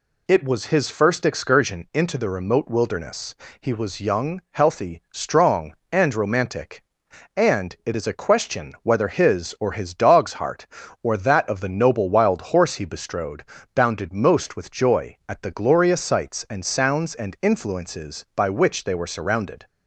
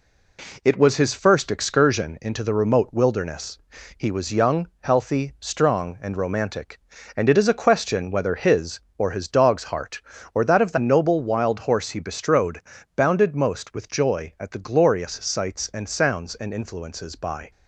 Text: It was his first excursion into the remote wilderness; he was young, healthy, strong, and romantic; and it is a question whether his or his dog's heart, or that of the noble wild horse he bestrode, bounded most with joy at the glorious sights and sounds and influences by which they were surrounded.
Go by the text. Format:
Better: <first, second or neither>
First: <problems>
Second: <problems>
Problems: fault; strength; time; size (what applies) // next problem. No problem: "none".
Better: first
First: none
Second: stops before "which they were surrounded"; at 17.5 s